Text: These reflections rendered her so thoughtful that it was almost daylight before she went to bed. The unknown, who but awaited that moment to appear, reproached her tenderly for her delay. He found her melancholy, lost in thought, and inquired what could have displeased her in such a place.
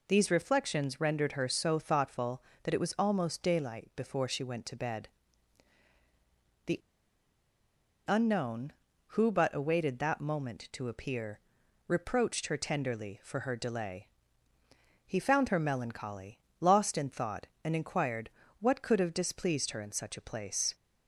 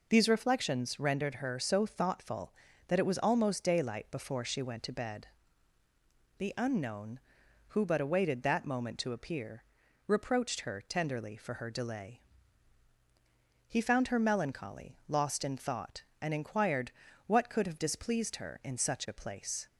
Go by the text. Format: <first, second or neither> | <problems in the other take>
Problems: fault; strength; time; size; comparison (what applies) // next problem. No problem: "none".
second | pauses between "The" and "unknown"; strong; at 6.7 s; 1.2 s long // pauses between "inquired" and "what"; slight; at 18.2 s; 0.32 s long; slight in the second